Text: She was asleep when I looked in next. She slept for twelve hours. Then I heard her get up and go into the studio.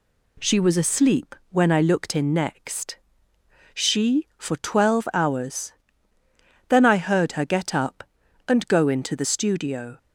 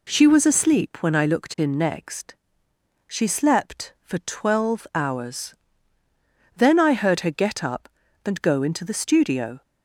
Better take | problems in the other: second | pauses between "asleep" and "when"; slight; at 1.3 s; 0.16 s long // skips "slept"; at 4.3 s

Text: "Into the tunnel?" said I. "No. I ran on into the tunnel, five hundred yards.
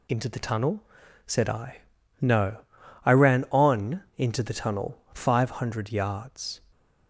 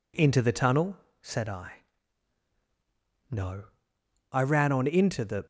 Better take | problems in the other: first | stops before "tunnel five hundred yards"; at 5.4 s

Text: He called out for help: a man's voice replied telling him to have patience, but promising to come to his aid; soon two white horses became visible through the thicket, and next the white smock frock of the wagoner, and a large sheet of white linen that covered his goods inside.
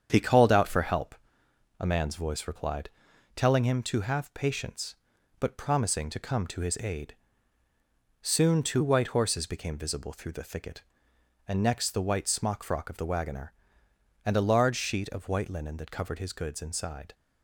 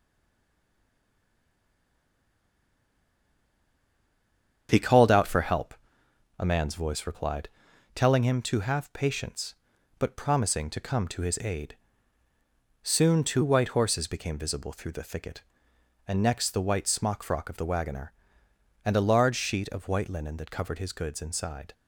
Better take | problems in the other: first | stays silent before the first word; strong; until 4.6 s; 4.6 s long // starts louder than the rest; strong; until 5.7 s; 8 dB; strong in the first // pauses between "replied" and "telling"; noticeable; at 7.4 s; 0.48 s long; noticeable in the first

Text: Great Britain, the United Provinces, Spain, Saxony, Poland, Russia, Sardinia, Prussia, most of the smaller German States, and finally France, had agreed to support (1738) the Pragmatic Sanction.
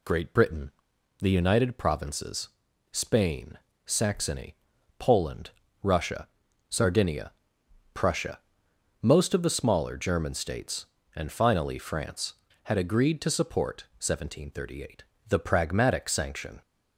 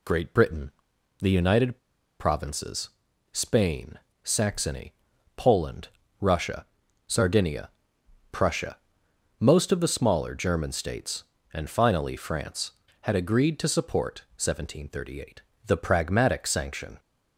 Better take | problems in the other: first | pauses between "United" and "Provinces"; at 1.7 s; 0.43 s long

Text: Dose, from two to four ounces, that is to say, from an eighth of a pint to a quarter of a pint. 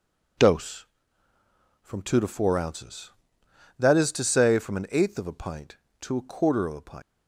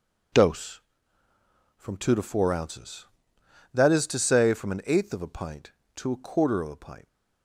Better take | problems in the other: second | leaves "pint" unfinished; at 7.0 s; 105 ms

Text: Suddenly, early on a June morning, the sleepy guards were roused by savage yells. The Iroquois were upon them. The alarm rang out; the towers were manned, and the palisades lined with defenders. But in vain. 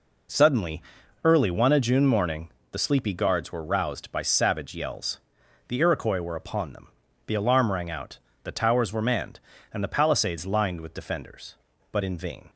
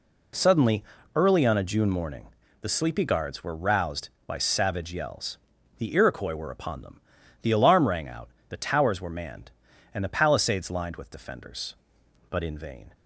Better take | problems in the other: second | says "one" for "on"; at 1.5 s

